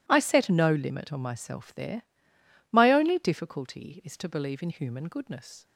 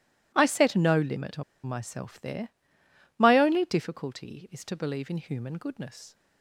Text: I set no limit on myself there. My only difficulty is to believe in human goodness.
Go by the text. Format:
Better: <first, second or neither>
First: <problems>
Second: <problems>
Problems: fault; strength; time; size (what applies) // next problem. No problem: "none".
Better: first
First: none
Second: pauses between "on" and "myself"; slight; at 1.4 s; 0.23 s long